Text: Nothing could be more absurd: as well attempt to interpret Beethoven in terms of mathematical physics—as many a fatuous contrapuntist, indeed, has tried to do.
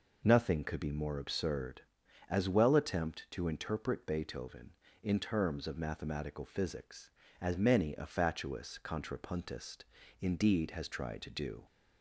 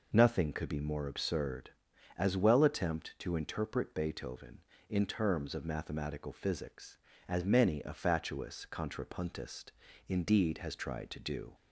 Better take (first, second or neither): neither